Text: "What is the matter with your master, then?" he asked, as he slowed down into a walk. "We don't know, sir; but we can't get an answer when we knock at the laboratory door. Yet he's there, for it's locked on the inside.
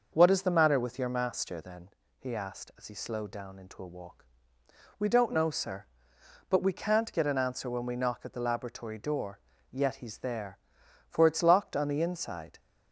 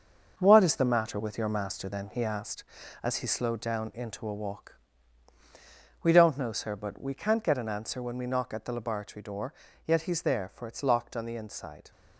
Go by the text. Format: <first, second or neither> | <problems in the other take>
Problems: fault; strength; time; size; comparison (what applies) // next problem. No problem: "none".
first | gets quieter; strong; throughout; 7.5 dB // starts louder than the rest; until 1.4 s; 6 dB; noticeable in the first